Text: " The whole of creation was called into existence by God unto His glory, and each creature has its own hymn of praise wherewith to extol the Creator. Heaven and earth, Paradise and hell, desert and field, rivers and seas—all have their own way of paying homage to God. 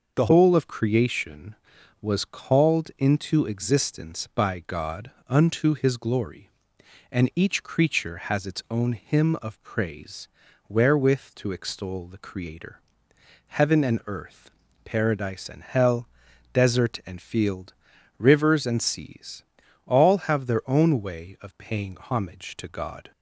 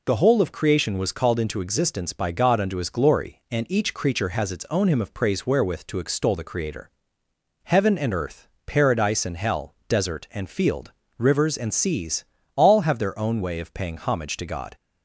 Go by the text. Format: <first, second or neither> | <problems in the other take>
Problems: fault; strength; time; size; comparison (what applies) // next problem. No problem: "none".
second | changes voice at "whole"; from 0.2 s on; 22.9 s long // pauses between "God" and "unto"; slight; at 5.1 s; 0.16 s long // pauses between "praise" and "wherewith"; at 10.2 s; 0.40 s long